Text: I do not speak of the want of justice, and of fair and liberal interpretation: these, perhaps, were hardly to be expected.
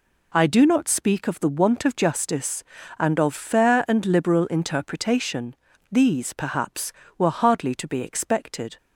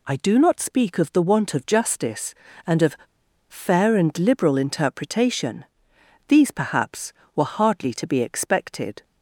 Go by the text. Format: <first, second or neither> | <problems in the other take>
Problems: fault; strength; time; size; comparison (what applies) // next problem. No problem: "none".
first | pauses between "of" and "fair"; noticeable; at 2.9 s; 0.53 s long